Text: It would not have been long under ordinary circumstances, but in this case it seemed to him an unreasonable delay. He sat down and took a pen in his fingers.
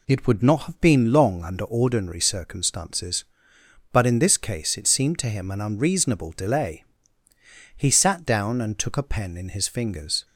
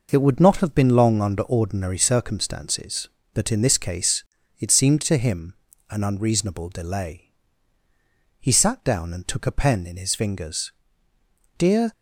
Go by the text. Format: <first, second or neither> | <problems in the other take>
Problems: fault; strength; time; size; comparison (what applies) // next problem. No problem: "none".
first | pauses between "case" and "it"; slight; at 4.2 s; 0.34 s long // pauses between "him" and "an"; slight; at 5.5 s; 0.36 s long // goes on to say "Dear"; slight; from 11.5 s on; 0.34 s long